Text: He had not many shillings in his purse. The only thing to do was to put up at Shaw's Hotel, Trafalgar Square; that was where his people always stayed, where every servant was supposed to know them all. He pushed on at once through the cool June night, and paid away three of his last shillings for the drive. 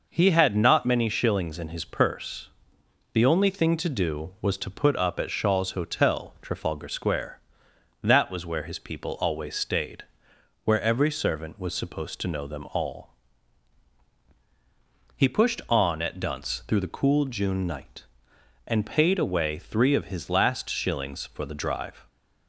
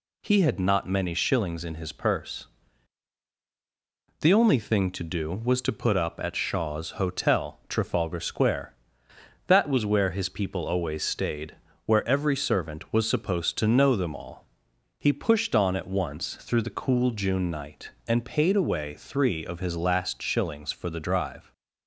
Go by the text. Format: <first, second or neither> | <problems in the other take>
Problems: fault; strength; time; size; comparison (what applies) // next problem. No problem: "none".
second | says "dunce" for "once"; at 16.1 s